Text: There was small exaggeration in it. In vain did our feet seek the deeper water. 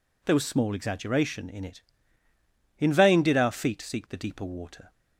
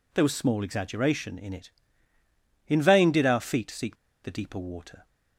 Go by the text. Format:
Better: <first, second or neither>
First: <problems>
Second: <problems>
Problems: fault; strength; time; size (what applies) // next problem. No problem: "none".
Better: first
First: none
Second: pauses between "seek" and "the"; slight; at 3.9 s; 0.27 s long